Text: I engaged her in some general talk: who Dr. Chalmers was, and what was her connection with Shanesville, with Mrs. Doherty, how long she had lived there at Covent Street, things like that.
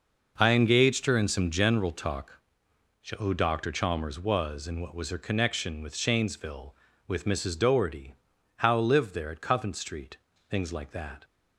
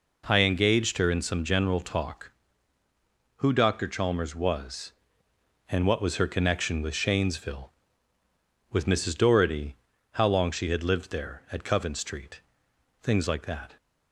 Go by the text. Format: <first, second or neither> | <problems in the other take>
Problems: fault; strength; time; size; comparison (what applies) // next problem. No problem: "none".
second | skips "long she had"; at 8.7 s